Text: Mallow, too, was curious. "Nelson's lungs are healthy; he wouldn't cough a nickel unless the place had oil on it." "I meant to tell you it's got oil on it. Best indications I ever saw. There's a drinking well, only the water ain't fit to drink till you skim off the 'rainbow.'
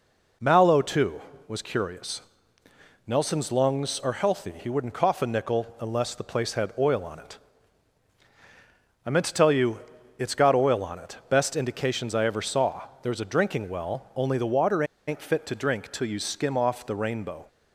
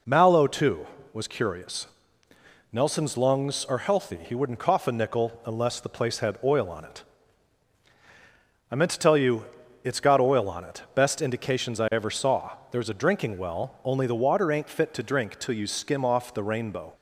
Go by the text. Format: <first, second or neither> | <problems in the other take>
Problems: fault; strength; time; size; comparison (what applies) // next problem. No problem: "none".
second | pauses between "you" and "it's"; at 9.7 s; 0.38 s long; also in the second // pauses between "water" and "ain't"; slight; at 14.8 s; 0.23 s long